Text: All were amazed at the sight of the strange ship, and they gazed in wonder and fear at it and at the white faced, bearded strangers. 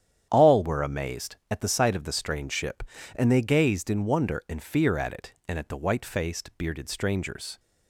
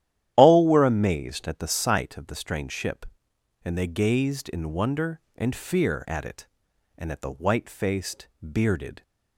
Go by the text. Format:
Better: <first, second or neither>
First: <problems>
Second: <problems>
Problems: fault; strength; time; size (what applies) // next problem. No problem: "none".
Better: first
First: starts louder than the rest; strong; until 1.3 s; 9.5 dB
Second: starts louder than the rest; strong; until 1.3 s; 11.5 dB // stops before "strangers"; at 9.0 s